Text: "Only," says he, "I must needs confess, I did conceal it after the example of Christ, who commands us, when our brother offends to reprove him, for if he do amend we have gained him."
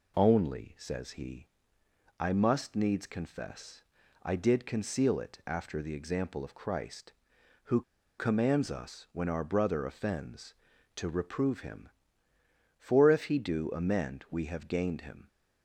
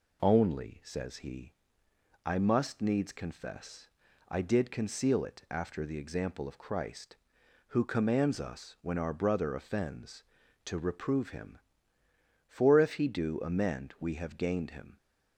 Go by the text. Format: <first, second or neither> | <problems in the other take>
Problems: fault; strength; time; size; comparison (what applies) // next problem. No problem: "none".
second | pauses between "who" and "commands"; at 7.8 s; 0.37 s long